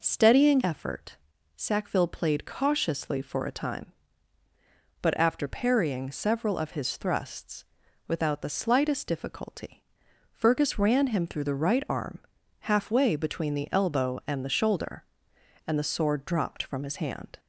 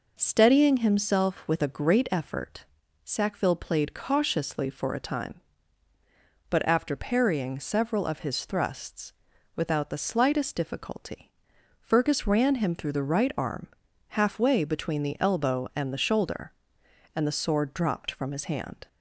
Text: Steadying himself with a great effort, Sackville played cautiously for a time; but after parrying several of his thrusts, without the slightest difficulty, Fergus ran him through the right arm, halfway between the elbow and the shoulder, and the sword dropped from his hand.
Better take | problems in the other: second | skips "himself with a great"; at 0.6 s

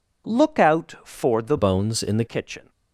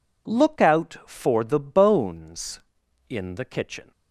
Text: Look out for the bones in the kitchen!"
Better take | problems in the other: second | changes voice from "bones" to "the"; from 1.5 to 2.2 s; 0.7 s long

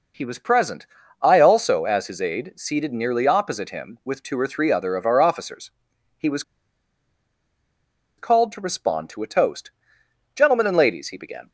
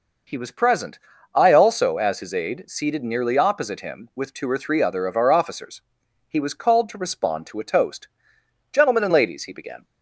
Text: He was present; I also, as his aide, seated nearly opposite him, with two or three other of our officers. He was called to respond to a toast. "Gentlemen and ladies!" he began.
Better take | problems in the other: second | pauses between "was" and "called"; strong; at 6.4 s; 1.7 s long

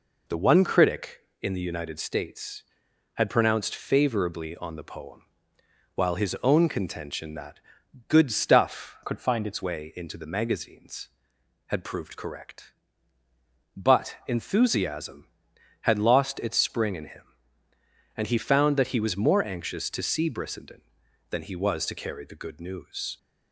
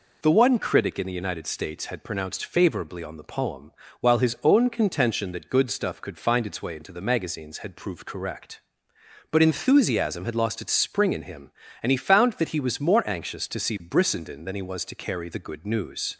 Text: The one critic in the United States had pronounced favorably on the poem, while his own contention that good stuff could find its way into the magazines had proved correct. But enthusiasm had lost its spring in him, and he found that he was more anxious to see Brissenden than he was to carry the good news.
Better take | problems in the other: second | pauses between "that" and "good"; noticeable; at 7.6 s; 0.48 s long // changes voice from "could" to "its"; from 9.0 to 9.6 s; 0.6 s long

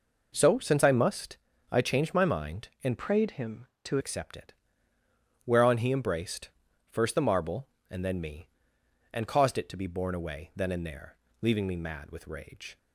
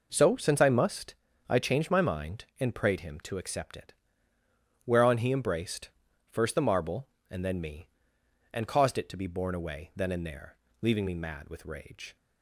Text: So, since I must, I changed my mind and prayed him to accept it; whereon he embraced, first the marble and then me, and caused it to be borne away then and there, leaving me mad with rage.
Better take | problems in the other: second | changes voice from "prayed" to "to"; from 2.9 to 3.9 s; 1.0 s long

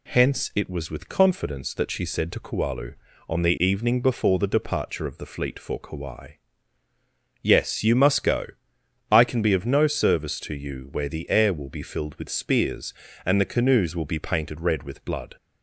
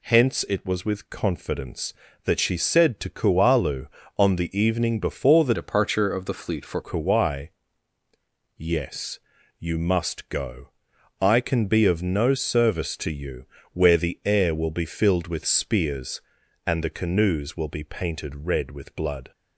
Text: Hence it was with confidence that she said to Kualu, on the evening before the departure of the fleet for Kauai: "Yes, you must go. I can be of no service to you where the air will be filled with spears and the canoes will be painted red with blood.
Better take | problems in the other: first | changes voice from "departure" to "for"; from 5.5 to 6.8 s; 1.3 s long // pauses between "you" and "where"; slight; at 13.4 s; 0.28 s long

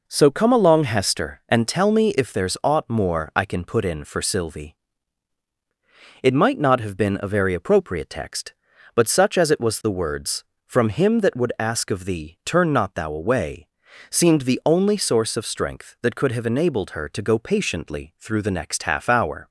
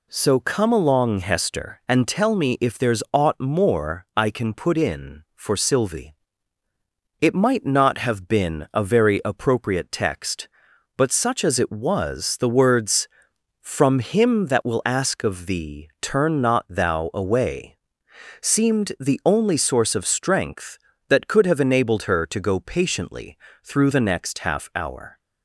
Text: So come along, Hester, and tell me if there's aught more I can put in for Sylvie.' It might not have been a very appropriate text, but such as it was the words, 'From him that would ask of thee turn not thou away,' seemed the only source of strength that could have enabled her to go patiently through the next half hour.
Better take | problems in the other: first | says "will" for "would"; at 14.6 s // pauses between "patiently" and "through"; slight; at 23.3 s; 0.26 s long

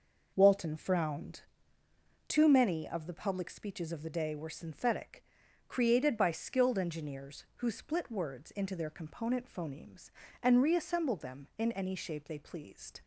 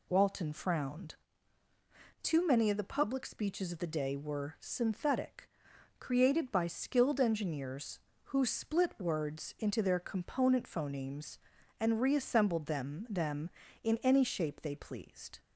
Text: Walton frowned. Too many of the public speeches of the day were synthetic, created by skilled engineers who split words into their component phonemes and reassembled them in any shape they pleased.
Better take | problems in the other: first | says "them" twice; at 13.0 s

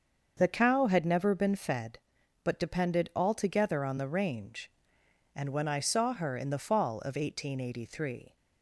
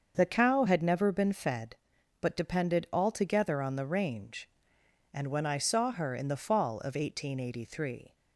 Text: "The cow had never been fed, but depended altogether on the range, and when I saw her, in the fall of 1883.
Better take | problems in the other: neither | starts louder than the rest; the same in both

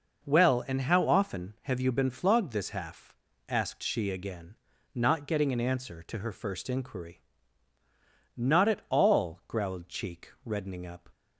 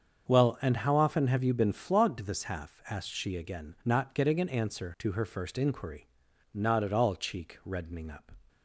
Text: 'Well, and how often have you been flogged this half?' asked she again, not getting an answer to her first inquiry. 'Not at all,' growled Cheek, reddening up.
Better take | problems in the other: first | starts louder than the rest; until 1.3 s; 7 dB // skips "growled"; at 7.1 s

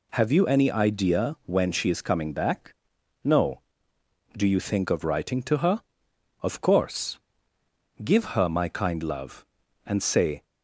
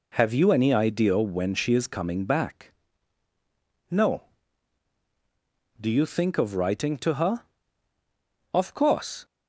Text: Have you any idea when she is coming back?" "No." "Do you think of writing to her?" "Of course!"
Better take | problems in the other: second | goes on to say "Give her my kind love and say"; strong; from 8.0 s on; 2.4 s long

